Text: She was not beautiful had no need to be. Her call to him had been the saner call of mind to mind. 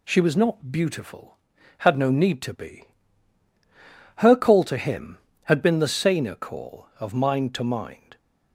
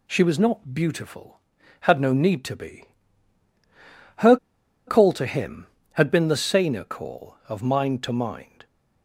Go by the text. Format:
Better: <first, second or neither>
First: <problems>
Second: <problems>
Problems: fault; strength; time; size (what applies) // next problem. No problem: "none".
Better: first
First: none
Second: pauses between "Her" and "call"; noticeable; at 4.3 s; 0.51 s long